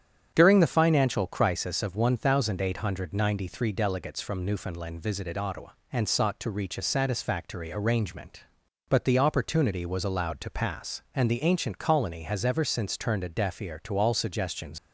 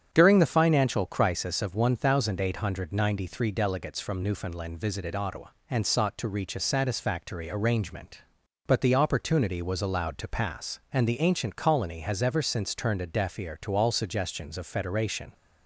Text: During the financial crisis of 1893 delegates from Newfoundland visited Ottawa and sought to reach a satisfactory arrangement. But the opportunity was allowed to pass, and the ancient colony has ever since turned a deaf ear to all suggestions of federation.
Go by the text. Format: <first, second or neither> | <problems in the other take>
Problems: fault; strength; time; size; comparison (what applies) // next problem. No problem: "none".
second | starts louder than the rest; strong; until 1.3 s; 8.5 dB; strong in the second // stops before "of federation"; at 14.7 s